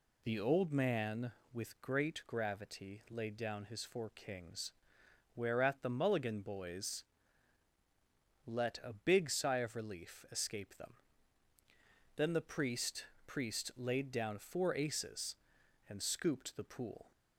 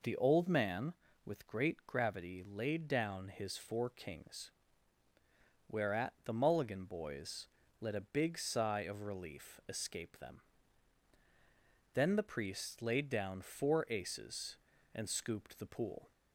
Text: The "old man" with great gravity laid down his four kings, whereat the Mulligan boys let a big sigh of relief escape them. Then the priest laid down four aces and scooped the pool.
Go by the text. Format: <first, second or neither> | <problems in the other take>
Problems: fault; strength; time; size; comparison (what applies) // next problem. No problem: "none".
second | pauses between "boys" and "let"; strong; at 7.0 s; 1.4 s long; slight in the second // says "priest" twice; at 13.2 s